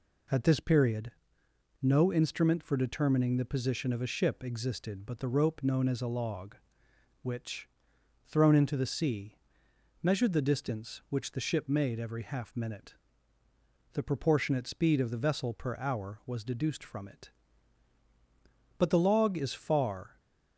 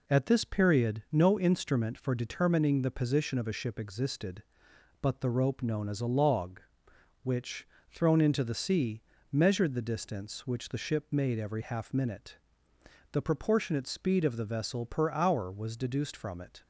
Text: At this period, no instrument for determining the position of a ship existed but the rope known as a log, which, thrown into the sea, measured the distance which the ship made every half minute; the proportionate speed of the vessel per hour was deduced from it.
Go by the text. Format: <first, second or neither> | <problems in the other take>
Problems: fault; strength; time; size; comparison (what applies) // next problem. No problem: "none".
second | goes on to say "But the log is far"; from 18.7 s on; 1.4 s long